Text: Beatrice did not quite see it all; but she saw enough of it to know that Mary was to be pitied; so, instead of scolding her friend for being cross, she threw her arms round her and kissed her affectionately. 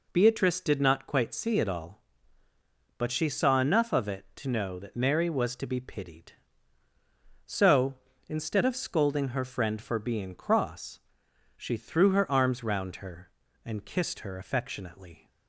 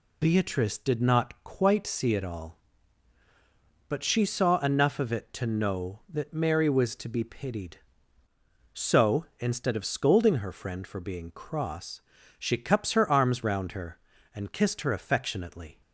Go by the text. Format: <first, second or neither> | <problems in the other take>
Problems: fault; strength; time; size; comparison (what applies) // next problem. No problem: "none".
first | says "cups" for "threw"; at 12.5 s